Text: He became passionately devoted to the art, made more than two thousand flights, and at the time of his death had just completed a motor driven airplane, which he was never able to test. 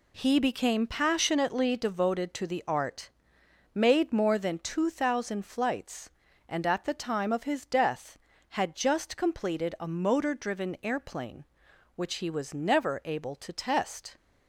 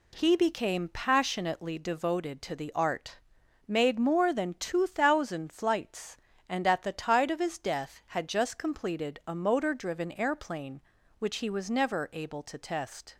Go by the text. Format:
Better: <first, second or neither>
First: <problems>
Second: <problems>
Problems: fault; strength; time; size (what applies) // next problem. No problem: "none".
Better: first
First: none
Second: says "tide" for "time"; at 6.9 s